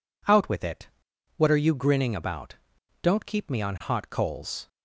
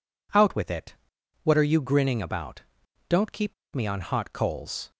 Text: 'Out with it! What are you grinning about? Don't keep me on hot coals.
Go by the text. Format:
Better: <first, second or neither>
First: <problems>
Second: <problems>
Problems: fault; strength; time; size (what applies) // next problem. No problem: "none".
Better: first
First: none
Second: pauses between "keep" and "me"; slight; at 3.5 s; 0.20 s long